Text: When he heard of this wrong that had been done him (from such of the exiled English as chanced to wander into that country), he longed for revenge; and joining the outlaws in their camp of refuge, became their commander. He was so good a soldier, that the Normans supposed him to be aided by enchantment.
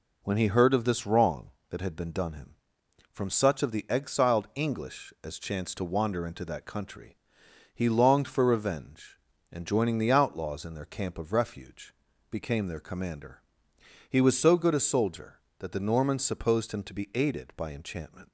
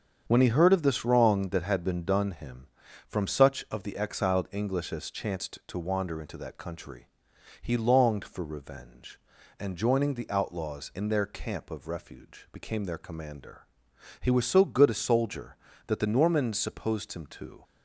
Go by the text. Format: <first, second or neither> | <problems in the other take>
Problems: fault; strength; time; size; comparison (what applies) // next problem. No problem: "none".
first | starts louder than the rest; strong; until 1.2 s; 7.5 dB // stops before "be aided by enchantment"; at 17.6 s